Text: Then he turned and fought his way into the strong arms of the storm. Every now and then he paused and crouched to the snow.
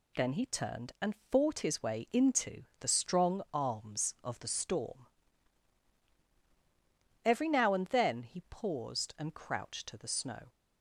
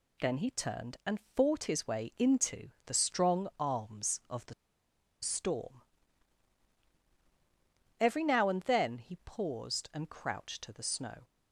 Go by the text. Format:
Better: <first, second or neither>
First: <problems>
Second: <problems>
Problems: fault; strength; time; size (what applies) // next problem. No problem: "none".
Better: first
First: pauses between "and" and "fought"; slight; at 1.1 s; 0.16 s long // pauses between "into" and "the"; slight; at 2.6 s; 0.16 s long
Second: pauses between "and" and "fought"; slight; at 1.1 s; 0.16 s long // pauses between "into" and "the"; slight; at 2.6 s; 0.16 s long // pauses between "the" and "storm"; noticeable; at 4.5 s; 0.68 s long